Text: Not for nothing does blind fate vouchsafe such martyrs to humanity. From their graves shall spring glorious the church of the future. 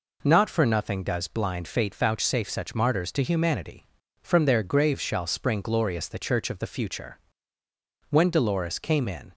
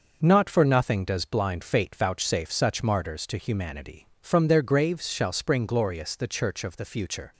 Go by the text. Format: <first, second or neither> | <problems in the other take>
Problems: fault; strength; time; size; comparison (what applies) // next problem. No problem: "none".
second | goes on to say "When Dolores came in"; noticeable; from 8.1 s on; 1.2 s long